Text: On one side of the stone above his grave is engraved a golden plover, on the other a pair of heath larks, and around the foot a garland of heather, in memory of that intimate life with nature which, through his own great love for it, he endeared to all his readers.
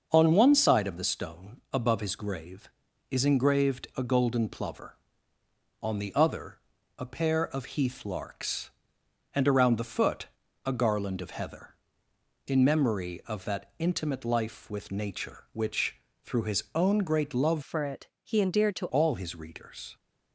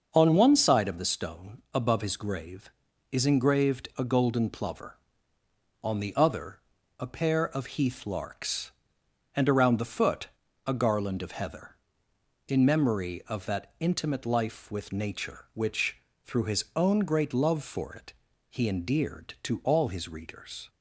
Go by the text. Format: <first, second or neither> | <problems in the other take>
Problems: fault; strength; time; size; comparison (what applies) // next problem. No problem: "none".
second | starts louder than the rest; until 1.1 s; 6 dB; also in the second // pauses between "other" and "a"; at 6.5 s; 0.38 s long; also in the second // pauses between "foot" and "a"; slight; at 10.2 s; 0.36 s long; slight in the second // changes voice from "for" to "to"; from 17.6 to 18.8 s; 1.2 s long